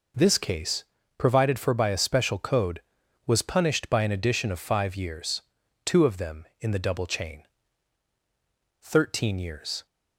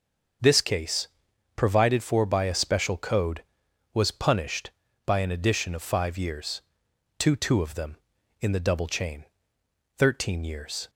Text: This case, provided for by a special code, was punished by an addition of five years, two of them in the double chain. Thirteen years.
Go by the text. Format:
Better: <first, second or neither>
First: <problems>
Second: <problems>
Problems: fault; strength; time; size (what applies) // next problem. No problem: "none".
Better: first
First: none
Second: starts louder than the rest; until 1.9 s; 6.5 dB // says "two" twice; at 7.3 s